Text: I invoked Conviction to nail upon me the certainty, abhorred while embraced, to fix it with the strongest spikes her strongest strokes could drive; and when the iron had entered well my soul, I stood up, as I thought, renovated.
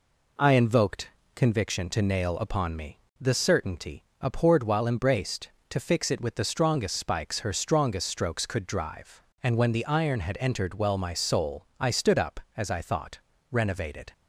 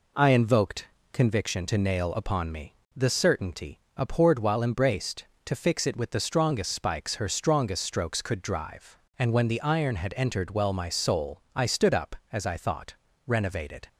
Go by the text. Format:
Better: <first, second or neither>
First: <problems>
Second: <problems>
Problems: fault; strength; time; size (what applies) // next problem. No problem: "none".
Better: neither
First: pauses between "invoked" and "Conviction"; slight; at 1.0 s; 0.26 s long // pauses between "me" and "the"; slight; at 3.0 s; 0.18 s long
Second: pauses between "invoked" and "Conviction"; slight; at 0.8 s; 0.26 s long // pauses between "me" and "the"; slight; at 2.7 s; 0.18 s long